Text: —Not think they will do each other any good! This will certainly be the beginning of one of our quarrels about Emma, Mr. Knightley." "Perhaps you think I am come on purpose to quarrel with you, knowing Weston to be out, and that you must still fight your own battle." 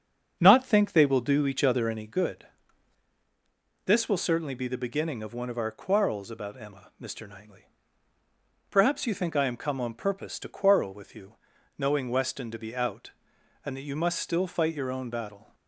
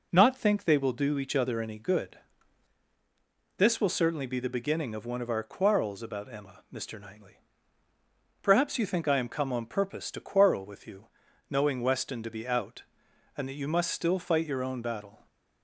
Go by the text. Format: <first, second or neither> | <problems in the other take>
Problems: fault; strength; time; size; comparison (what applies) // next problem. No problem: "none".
second | starts louder than the rest; until 2.2 s; 7 dB